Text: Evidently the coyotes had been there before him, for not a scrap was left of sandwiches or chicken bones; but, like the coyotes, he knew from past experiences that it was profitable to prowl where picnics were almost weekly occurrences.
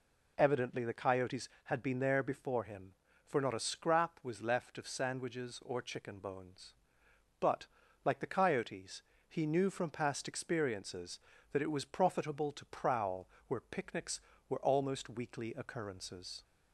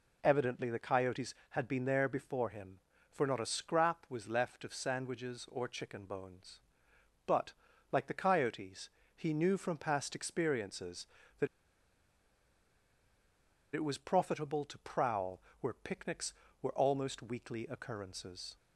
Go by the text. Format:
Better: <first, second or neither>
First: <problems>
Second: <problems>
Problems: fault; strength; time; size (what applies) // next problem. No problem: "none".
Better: first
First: pauses between "prowl" and "where"; slight; at 13.2 s; 0.20 s long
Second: pauses between "that" and "it"; strong; at 11.4 s; 2.2 s long // pauses between "prowl" and "where"; slight; at 15.3 s; 0.20 s long